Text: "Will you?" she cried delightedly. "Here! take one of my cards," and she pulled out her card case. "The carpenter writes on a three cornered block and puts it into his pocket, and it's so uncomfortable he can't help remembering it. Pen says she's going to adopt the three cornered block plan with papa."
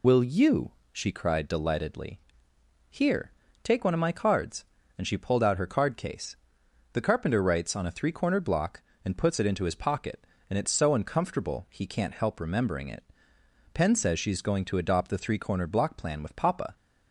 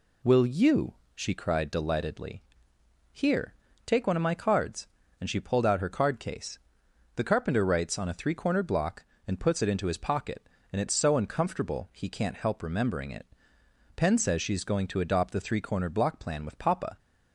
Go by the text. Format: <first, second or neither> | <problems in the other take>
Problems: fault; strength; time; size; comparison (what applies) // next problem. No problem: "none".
second | loses the start of "Will"; at 0.0 s; 30 ms